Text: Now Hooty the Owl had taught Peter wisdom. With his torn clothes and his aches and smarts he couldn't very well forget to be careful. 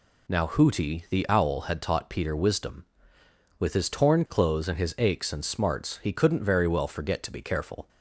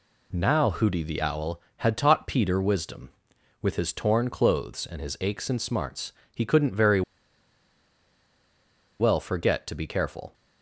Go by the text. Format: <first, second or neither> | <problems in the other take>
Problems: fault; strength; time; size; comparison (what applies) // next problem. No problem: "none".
first | pauses between "smarts" and "he"; slight; at 6.1 s; 0.20 s long // pauses between "very" and "well"; strong; at 7.0 s; 1.9 s long